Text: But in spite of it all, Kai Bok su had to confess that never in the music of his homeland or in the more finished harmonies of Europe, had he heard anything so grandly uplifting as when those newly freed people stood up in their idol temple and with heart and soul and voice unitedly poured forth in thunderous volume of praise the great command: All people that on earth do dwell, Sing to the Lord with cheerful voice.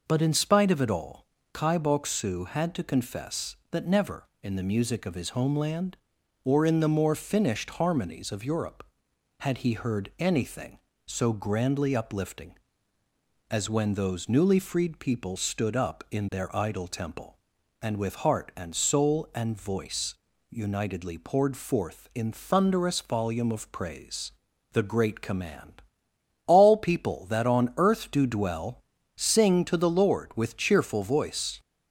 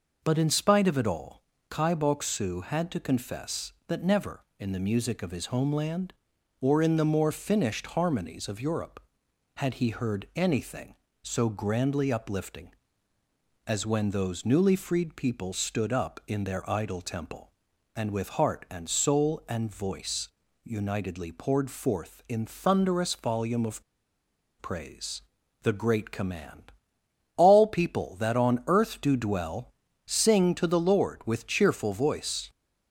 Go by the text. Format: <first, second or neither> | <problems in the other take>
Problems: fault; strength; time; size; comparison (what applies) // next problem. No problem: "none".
first | pauses between "voice" and "unitedly"; slight; at 20.2 s; 0.36 s long; slight in the first // pauses between "of" and "praise"; noticeable; at 23.8 s; 0.78 s long // pauses between "praise" and "the"; at 25.2 s; 0.40 s long; also in the first